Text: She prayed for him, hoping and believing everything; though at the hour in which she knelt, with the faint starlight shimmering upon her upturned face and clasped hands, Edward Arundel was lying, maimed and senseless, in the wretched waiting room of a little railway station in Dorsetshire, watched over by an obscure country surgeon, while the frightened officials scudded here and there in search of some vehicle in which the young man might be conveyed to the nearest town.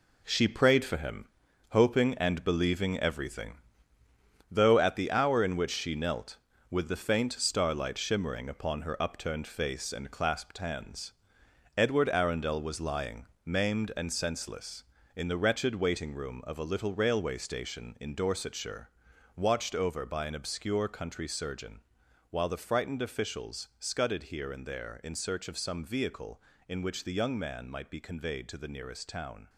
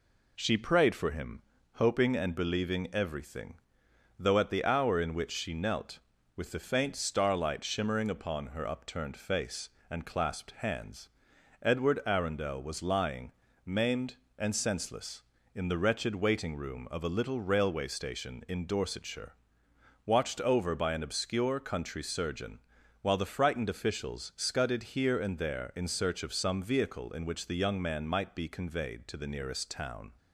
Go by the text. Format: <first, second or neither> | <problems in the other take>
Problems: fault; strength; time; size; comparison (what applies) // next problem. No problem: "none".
second | gets quieter; strong; throughout; 8 dB